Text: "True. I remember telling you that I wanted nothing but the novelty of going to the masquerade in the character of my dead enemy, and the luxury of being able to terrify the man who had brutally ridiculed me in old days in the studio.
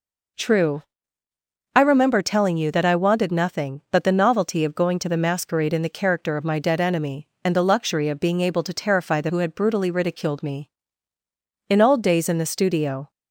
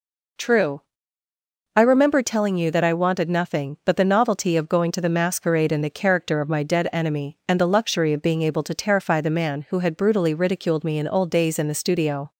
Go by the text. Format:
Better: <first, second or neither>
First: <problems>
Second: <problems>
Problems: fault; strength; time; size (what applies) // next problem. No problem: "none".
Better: second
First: skips "man"; at 9.2 s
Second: none